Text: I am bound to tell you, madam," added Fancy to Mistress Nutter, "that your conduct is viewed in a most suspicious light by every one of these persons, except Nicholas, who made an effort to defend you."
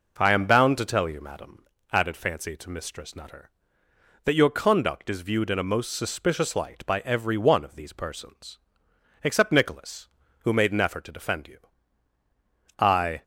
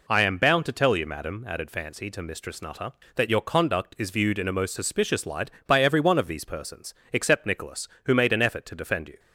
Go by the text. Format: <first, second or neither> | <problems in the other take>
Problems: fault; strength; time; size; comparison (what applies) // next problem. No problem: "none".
second | goes on to say "I"; slight; from 12.7 s on; 0.44 s long